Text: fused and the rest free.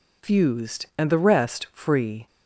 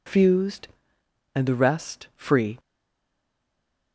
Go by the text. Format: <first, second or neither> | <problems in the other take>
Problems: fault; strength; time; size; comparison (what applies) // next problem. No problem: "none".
first | stays silent after the last word; noticeable; from 2.5 s on; 1.4 s long